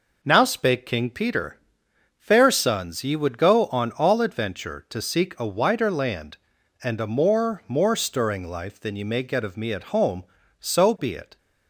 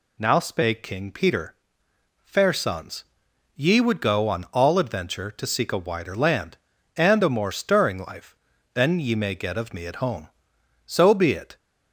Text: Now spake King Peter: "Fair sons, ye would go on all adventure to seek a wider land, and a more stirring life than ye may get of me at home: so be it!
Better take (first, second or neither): second